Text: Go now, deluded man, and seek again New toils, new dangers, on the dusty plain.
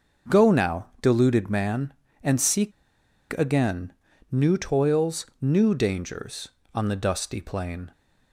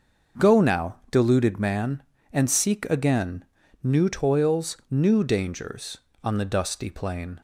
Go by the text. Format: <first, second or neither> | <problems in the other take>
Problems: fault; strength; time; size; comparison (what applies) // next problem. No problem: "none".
second | starts louder than the rest; noticeable; until 1.4 s; 6 dB // pauses between "seek" and "again"; noticeable; at 2.7 s; 0.66 s long // pauses between "again" and "New"; at 3.9 s; 0.38 s long; also in the second